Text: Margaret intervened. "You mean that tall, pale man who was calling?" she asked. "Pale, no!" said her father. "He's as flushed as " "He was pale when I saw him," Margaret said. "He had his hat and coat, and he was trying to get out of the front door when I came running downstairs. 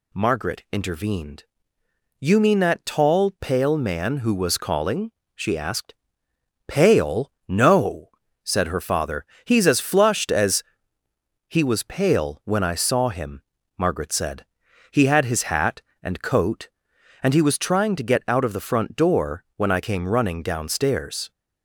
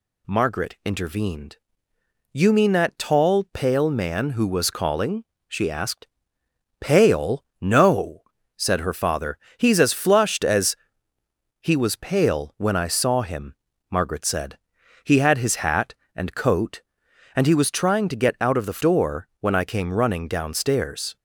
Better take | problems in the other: first | skips "front"; at 18.7 s

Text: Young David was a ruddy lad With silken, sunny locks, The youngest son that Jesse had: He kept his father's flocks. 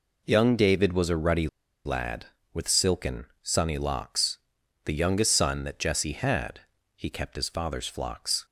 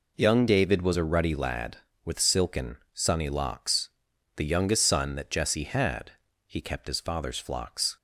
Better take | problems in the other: second | pauses between "ruddy" and "lad"; slight; at 1.4 s; 0.36 s long

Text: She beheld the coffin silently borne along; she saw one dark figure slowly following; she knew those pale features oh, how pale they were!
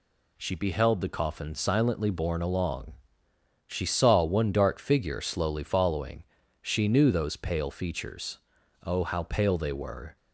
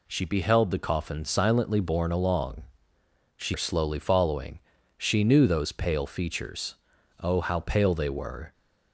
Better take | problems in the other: first | skips "saw one dark figure"; at 3.5 s // pauses between "features" and "oh"; noticeable; at 6.7 s; 0.46 s long; noticeable in the first

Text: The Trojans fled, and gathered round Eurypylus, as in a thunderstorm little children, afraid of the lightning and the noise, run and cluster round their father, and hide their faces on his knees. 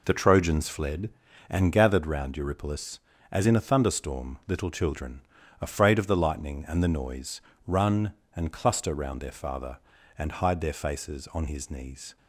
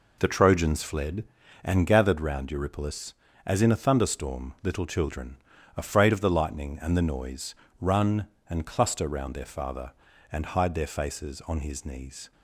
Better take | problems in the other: neither | none

